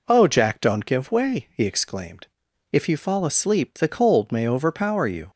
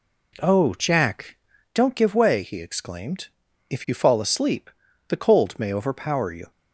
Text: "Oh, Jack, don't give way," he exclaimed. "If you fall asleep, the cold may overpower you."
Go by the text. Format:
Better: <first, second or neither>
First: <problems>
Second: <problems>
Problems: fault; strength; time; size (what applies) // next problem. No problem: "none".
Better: first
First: none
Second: gets quieter; noticeable; throughout; 5 dB